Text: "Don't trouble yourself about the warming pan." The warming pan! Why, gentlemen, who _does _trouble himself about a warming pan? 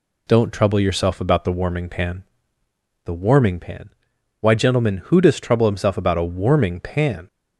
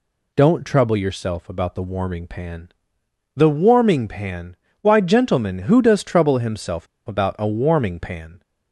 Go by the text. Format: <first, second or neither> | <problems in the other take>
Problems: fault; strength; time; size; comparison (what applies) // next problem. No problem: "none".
first | pauses between "himself" and "about"; slight; at 6.8 s; 0.21 s long